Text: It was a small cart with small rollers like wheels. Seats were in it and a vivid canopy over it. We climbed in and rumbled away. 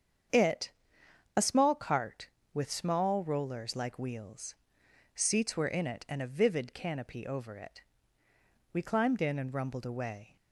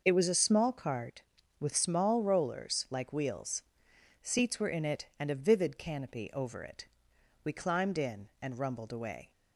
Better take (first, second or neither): second